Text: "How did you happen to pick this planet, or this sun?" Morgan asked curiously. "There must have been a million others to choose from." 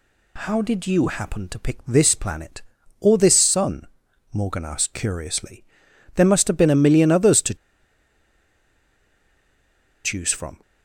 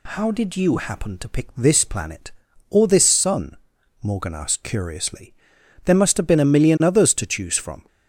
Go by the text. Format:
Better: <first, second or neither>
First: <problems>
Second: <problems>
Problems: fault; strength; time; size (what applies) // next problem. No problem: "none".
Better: second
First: pauses between "to" and "choose"; strong; at 7.5 s; 2.4 s long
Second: none